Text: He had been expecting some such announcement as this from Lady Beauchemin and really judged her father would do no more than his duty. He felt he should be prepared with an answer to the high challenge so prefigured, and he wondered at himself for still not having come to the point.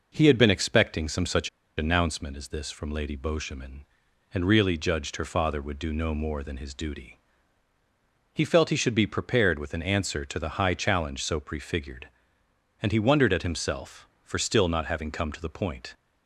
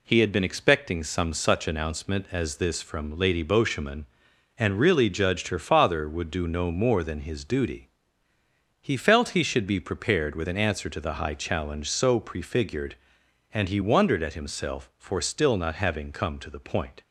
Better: second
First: pauses between "such" and "announcement"; slight; at 1.4 s; 0.28 s long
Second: none

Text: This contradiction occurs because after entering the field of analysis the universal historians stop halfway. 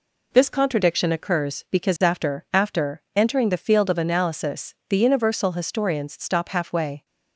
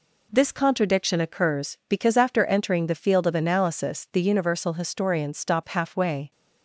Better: second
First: says "after" twice; at 2.5 s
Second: none

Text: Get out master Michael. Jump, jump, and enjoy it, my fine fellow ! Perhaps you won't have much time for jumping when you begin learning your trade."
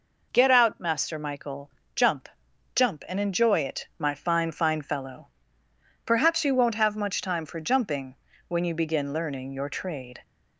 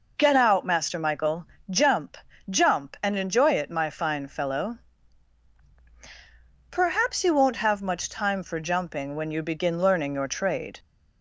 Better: second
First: says "fine" twice; at 4.5 s // pauses between "jumping" and "when"; slight; at 8.1 s; 0.32 s long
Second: none

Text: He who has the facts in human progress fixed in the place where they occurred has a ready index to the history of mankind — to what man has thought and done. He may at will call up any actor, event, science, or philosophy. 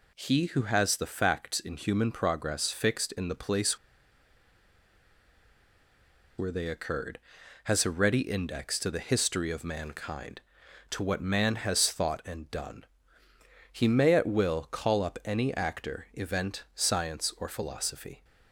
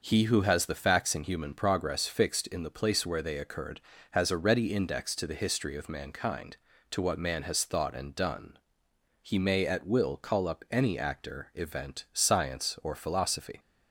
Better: second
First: pauses between "place" and "where"; strong; at 3.7 s; 2.5 s long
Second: none

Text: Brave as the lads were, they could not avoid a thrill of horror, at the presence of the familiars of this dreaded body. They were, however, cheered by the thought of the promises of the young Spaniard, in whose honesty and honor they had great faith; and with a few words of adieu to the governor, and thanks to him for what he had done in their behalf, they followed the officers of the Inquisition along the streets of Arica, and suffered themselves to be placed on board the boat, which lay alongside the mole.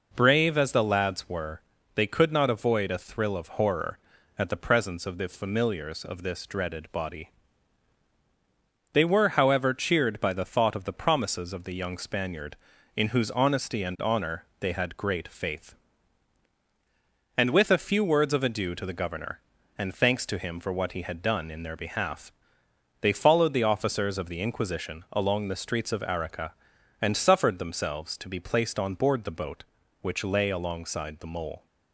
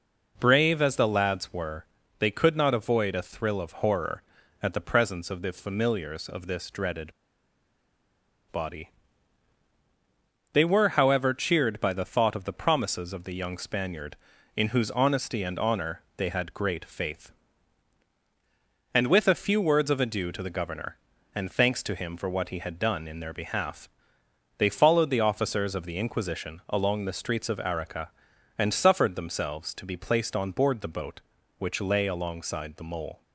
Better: first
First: pauses between "honor" and "they"; slight; at 14.4 s; 0.16 s long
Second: pauses between "dreaded" and "body"; strong; at 7.1 s; 1.3 s long // pauses between "honor" and "they"; slight; at 16.0 s; 0.16 s long

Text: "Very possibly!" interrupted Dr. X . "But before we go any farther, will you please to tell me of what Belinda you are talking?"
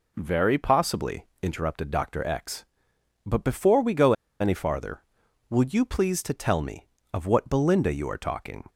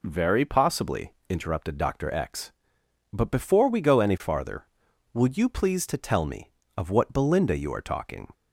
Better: second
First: pauses between "go" and "any"; slight; at 4.1 s; 0.28 s long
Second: none

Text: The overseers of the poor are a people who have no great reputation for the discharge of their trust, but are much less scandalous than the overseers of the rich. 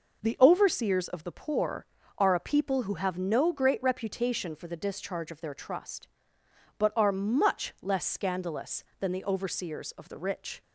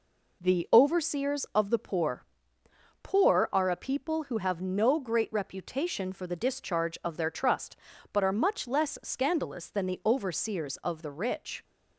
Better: first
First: none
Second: says "poor" twice; at 3.0 s

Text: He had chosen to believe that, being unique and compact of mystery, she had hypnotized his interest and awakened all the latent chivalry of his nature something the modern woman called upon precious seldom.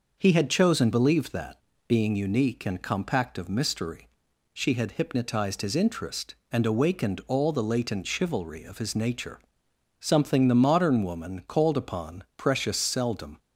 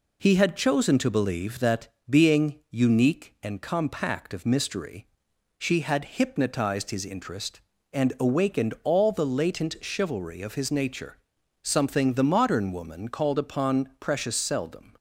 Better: second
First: skips "to"; at 0.9 s // pauses between "nature" and "something"; noticeable; at 9.3 s; 0.60 s long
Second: pauses between "nature" and "something"; noticeable; at 11.1 s; 0.46 s long

